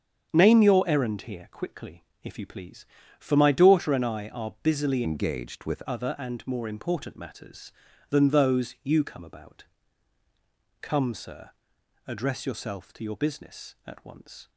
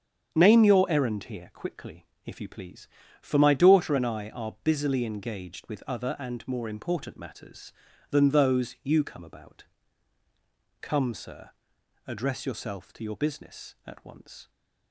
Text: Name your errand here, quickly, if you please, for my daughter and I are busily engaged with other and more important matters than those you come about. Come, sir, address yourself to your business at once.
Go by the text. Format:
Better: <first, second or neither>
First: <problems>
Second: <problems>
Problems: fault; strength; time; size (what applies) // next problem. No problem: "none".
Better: second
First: starts louder than the rest; strong; until 1.3 s; 7.5 dB // changes voice from "engaged" to "with"; from 5.0 to 5.8 s; 0.8 s long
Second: starts louder than the rest; strong; until 1.3 s; 7.5 dB